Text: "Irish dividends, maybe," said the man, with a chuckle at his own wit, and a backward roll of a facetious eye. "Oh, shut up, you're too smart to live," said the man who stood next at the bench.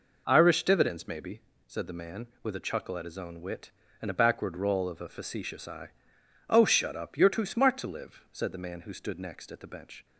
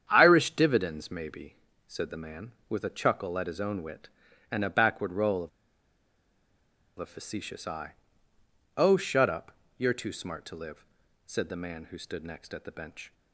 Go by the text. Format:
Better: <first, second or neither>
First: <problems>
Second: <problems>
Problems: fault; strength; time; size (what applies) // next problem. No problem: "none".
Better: first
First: none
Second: starts louder than the rest; strong; until 1.1 s; 8.5 dB // pauses between "of" and "a"; strong; at 5.4 s; 1.4 s long